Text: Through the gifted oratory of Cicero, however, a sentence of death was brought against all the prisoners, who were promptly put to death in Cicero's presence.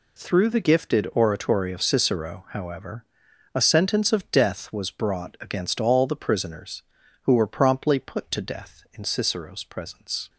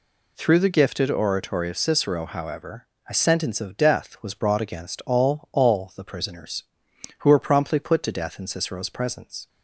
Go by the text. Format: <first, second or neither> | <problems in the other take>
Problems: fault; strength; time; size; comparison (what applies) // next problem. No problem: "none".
first | says "all" twice; at 5.5 s